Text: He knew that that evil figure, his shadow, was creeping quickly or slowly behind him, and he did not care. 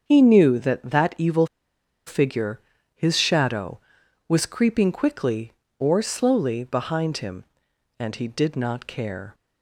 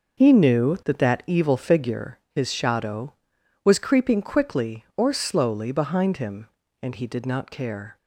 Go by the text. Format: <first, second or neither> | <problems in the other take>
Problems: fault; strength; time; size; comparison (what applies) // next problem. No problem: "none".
second | starts louder than the rest; until 1.0 s; 7 dB; noticeable in the second // pauses between "evil" and "figure"; noticeable; at 1.4 s; 0.60 s long